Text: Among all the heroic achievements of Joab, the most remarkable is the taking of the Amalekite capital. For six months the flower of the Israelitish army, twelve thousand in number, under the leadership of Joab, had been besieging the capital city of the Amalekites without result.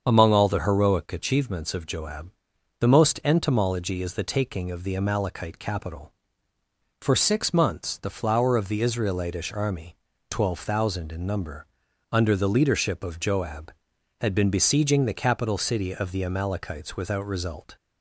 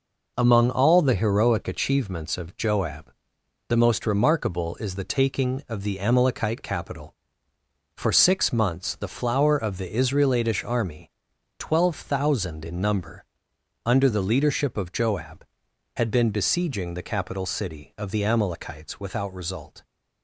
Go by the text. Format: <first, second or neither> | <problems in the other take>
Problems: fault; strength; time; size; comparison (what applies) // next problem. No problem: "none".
second | starts louder than the rest; until 1.0 s; 7 dB // says "entomology" for "remarkable"; at 3.2 s